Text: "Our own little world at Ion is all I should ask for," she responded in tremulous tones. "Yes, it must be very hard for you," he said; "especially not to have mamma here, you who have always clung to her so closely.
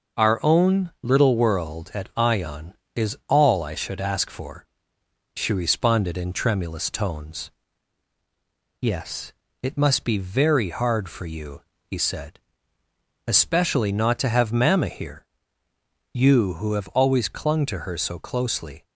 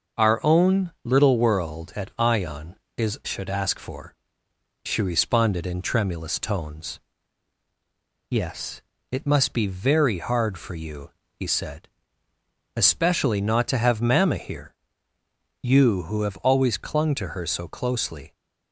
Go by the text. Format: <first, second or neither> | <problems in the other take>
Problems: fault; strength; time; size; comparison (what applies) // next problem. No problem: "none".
first | starts louder than the rest; noticeable; until 1.3 s; 6 dB // skips "all I"; at 3.2 s